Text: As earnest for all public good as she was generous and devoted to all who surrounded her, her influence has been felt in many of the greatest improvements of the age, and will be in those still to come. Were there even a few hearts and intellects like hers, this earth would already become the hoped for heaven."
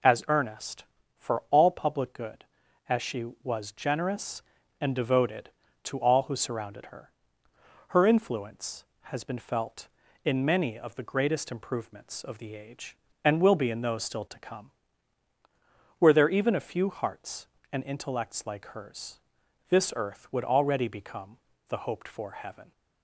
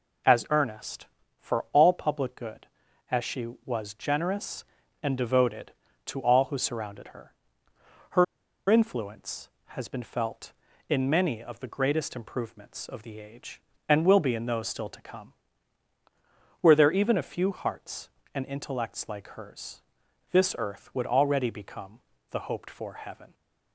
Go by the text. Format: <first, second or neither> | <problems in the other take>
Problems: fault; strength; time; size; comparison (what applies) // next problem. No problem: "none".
first | pauses between "her" and "influence"; at 8.2 s; 0.45 s long // pauses between "become" and "the"; slight; at 21.9 s; 0.30 s long; slight in the first